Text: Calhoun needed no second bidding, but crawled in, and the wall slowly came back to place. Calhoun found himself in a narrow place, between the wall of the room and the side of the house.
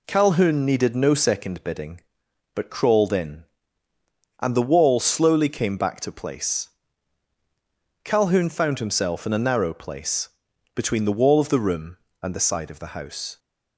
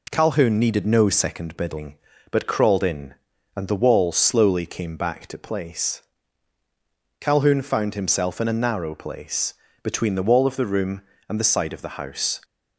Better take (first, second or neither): neither